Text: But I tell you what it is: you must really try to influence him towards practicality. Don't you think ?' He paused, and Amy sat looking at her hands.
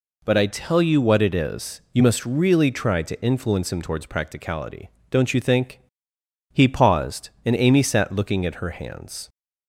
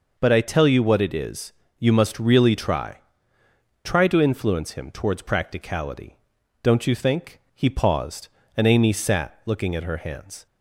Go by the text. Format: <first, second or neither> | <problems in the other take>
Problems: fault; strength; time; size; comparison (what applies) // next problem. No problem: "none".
first | says "try" twice; at 3.8 s